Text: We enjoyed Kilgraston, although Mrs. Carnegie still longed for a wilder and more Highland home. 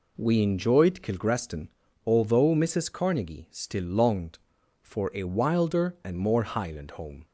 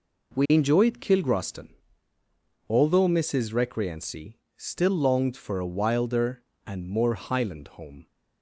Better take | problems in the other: first | says "Recreancy" for "Carnegie"; at 3.5 s

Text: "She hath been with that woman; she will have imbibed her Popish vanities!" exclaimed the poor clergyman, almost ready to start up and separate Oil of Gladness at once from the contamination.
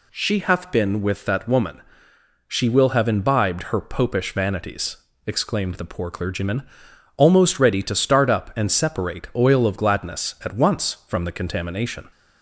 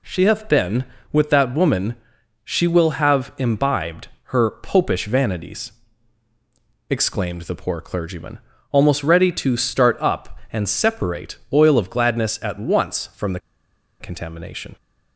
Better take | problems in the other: first | pauses between "imbibed" and "her"; slight; at 4.0 s; 0.16 s long // pauses between "the" and "contamination"; noticeable; at 13.3 s; 0.61 s long

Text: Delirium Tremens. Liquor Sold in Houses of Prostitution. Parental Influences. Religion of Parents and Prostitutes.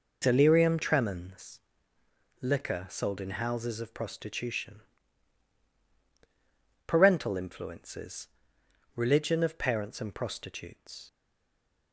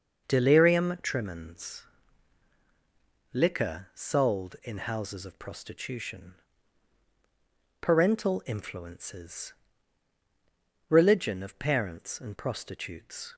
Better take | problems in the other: second | stays silent after the last word; slight; from 11.0 s on; 0.9 s long

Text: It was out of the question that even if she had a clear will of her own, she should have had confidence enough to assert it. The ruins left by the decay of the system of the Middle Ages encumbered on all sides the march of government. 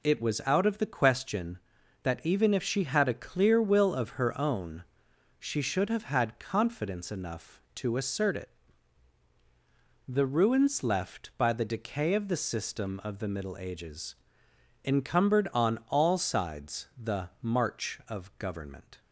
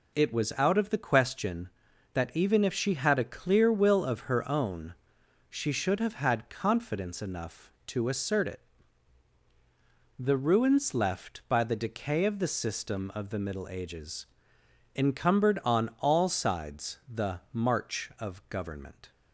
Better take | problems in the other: neither | pauses between "Ages" and "encumbered"; noticeable; the same in both

